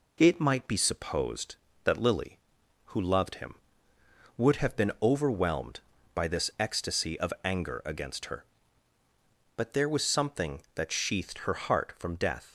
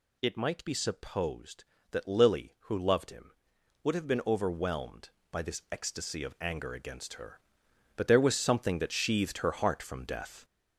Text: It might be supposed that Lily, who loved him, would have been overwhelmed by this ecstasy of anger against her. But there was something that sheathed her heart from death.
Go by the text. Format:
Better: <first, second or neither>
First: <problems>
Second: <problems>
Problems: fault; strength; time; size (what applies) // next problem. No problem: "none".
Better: first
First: none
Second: gets louder; noticeable; throughout; 6 dB